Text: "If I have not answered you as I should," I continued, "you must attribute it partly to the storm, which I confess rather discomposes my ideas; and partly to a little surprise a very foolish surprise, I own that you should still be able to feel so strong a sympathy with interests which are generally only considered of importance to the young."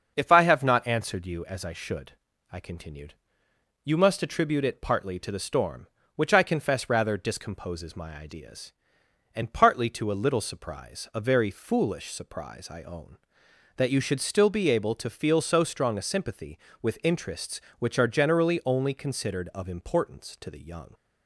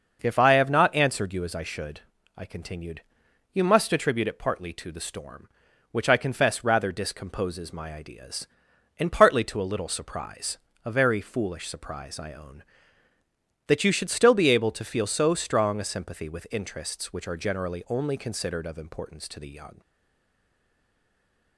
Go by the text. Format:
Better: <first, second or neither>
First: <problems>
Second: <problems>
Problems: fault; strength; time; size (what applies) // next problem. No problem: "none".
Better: first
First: starts louder than the rest; until 1.1 s; 6.5 dB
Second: starts louder than the rest; until 1.2 s; 6 dB // pauses between "surprise" and "a"; slight; at 10.5 s; 0.26 s long // stays silent after the last word; noticeable; from 19.8 s on; 1.7 s long